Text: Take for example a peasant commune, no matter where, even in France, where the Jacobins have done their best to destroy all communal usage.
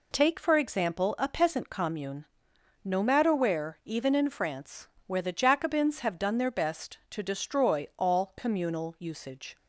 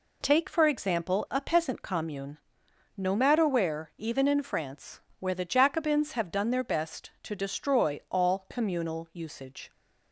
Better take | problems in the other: neither | none

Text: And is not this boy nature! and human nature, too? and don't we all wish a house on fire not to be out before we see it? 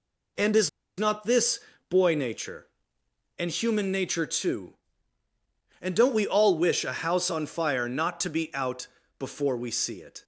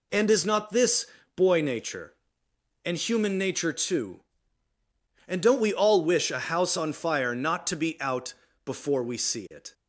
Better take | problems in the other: second | pauses between "is" and "not"; slight; at 0.6 s; 0.29 s long // pauses between "this" and "boy"; slight; at 1.5 s; 0.30 s long; slight in the second // pauses between "out" and "before"; slight; at 8.8 s; 0.30 s long; slight in the second

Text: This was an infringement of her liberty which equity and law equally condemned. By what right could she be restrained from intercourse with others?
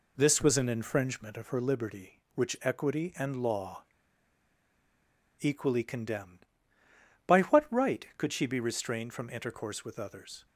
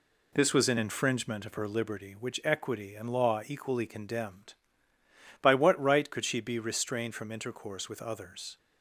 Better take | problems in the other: second | pauses between "law" and "equally"; strong; at 3.8 s; 1.5 s long

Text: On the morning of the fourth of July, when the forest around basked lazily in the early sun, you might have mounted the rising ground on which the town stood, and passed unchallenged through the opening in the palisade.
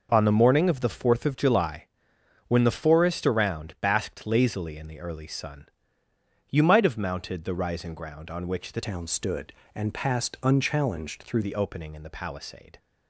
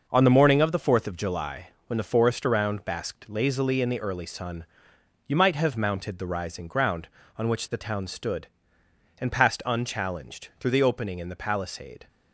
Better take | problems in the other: second | changes voice from "town" to "through"; from 8.8 to 11.4 s; 2.6 s long

